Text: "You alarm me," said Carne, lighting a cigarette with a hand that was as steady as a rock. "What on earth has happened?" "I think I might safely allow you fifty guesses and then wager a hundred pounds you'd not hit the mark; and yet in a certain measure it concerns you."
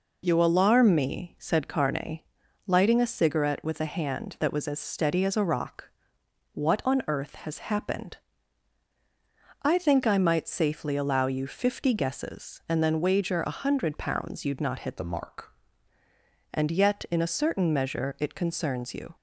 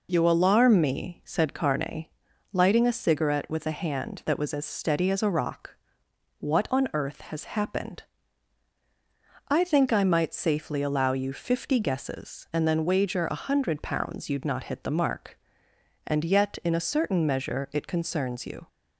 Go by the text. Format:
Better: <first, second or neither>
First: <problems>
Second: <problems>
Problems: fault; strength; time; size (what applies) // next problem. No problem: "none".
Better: second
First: changes voice from "the" to "mark"; from 14.9 to 15.5 s; 0.6 s long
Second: none